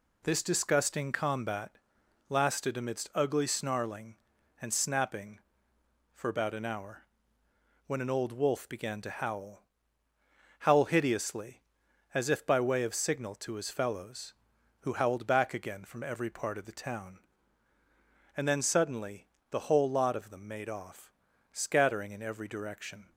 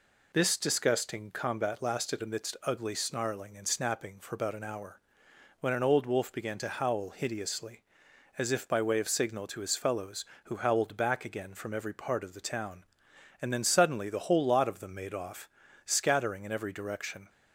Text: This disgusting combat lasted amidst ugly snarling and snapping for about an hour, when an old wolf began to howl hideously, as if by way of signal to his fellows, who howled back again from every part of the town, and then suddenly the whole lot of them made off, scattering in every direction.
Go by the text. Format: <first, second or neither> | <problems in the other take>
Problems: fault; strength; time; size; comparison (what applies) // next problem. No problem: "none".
second | pauses between "combat" and "lasted"; noticeable; at 1.7 s; 0.50 s long // says "howl" twice; at 10.6 s // pauses between "suddenly" and "the"; slight; at 19.2 s; 0.24 s long